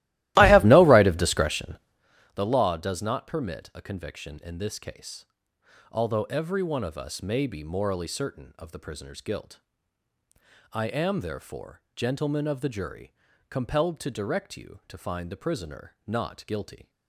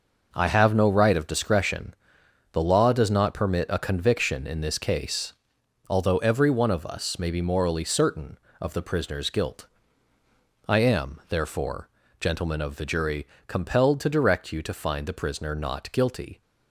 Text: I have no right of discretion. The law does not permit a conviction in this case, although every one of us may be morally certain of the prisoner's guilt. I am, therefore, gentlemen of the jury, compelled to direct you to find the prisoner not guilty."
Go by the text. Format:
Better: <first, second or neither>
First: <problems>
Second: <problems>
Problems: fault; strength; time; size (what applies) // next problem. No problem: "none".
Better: second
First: starts louder than the rest; strong; until 2.2 s; 16.5 dB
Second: none